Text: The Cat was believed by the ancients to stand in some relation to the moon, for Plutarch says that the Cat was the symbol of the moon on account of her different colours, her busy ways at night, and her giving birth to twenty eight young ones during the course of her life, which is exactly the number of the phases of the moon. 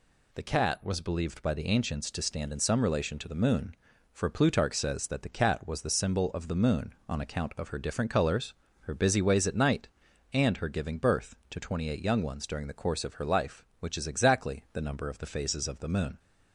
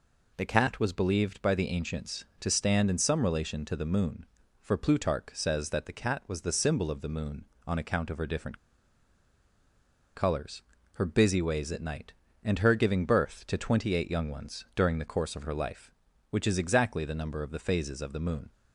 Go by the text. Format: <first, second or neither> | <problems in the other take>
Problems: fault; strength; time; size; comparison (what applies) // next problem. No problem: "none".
first | pauses between "different" and "colours"; strong; at 8.5 s; 1.5 s long